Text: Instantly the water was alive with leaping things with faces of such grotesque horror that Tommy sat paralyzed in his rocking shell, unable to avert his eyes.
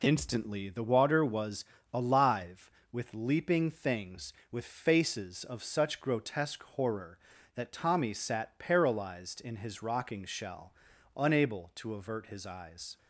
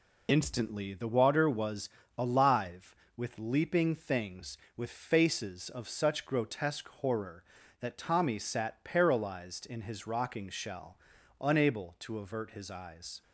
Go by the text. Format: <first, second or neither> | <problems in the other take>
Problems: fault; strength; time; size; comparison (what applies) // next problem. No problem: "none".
first | loses the start of "Instantly"; at 0.2 s; 35 ms // pauses between "was" and "alive"; slight; at 1.8 s; 0.30 s long; slight in the first